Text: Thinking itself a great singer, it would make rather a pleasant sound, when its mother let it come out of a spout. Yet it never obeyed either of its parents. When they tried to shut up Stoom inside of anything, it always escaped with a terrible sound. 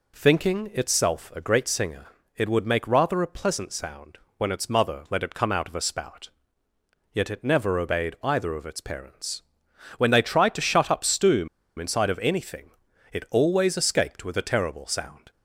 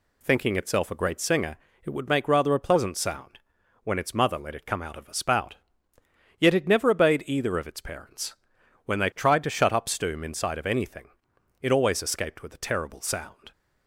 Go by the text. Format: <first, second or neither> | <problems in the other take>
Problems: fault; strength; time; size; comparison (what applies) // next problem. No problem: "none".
second | pauses between "Stoom" and "inside"; slight; at 11.4 s; 0.31 s long